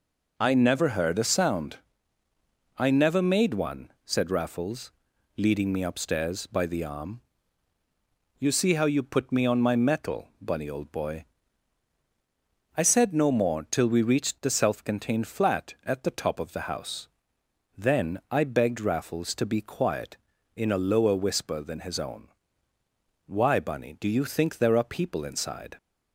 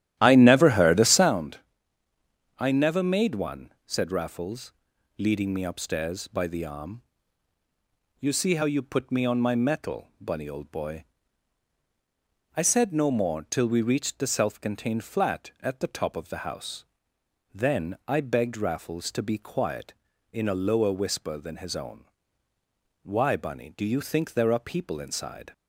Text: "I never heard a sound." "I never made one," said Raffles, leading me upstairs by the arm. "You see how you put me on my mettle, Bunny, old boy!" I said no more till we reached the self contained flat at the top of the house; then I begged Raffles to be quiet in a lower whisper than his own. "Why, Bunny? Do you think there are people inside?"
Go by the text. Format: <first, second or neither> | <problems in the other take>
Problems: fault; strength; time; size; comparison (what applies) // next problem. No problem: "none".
first | starts louder than the rest; strong; until 1.4 s; 12.5 dB